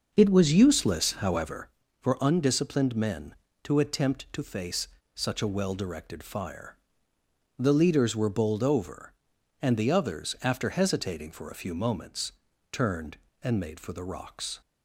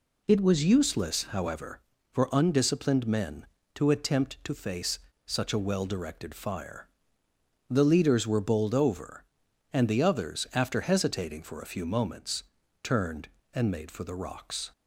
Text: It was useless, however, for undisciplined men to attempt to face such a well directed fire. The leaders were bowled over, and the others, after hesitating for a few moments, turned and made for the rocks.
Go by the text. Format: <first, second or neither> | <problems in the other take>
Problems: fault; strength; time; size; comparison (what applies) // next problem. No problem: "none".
second | starts louder than the rest; until 1.7 s; 6 dB // pauses between "face" and "such"; slight; at 4.8 s; 0.28 s long; slight in the second